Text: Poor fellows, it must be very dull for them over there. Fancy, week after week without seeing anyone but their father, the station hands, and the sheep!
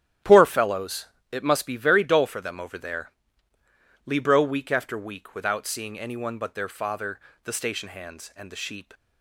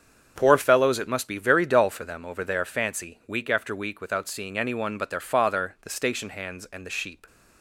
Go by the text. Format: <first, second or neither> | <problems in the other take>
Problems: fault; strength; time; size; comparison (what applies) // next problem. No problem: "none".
second | starts louder than the rest; strong; until 1.5 s; 11.5 dB; strong in the second // says "Libro" for "Fancy"; at 4.0 s